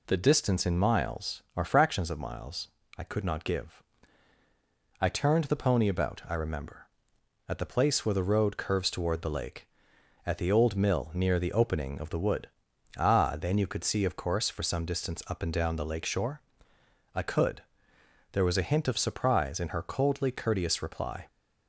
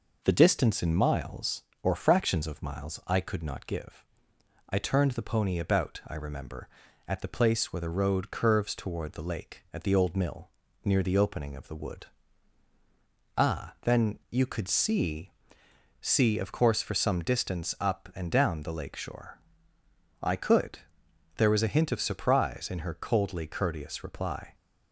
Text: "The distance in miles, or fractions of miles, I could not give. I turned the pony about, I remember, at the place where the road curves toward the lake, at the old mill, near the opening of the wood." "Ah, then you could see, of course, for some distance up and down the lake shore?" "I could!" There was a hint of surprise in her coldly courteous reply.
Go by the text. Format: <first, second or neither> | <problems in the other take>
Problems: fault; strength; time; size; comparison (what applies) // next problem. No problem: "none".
first | says "see" twice; at 16.0 s